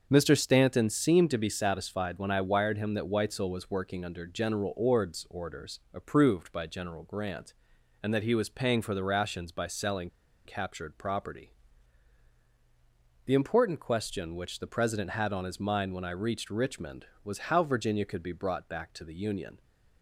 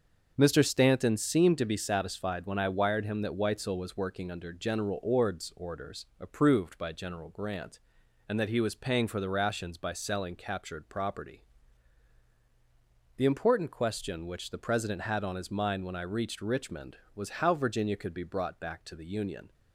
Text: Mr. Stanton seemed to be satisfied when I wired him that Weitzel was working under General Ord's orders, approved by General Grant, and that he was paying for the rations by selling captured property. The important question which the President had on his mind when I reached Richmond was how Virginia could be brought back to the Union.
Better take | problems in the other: second | starts louder than the rest; until 1.1 s; 6.5 dB; also in the second // pauses between "selling" and "captured"; slight; at 10.0 s; 0.35 s long

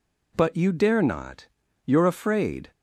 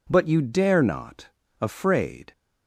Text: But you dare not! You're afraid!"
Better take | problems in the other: first | skips "You're"; at 1.4 s

